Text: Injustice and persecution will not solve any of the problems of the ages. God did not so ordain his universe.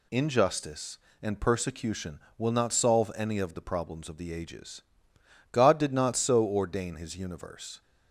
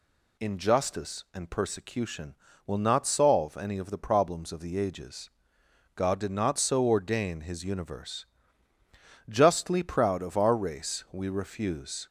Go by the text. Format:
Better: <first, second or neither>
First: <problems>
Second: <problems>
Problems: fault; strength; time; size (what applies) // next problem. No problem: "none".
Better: first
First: none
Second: goes on to say "Justly proud of our race we refuse"; strong; from 9.2 s on; 2.7 s long